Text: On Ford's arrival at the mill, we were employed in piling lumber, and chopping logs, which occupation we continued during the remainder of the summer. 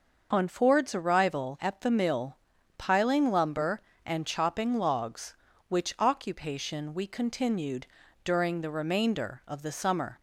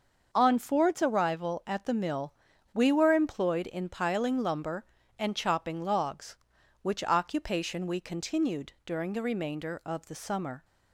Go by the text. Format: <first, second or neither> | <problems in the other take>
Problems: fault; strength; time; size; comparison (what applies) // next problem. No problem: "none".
second | starts louder than the rest; noticeable; until 1.3 s; 6 dB; also in the second // skips "we were employed in"; at 2.5 s // pauses between "continued" and "during"; slight; at 7.8 s; 0.36 s long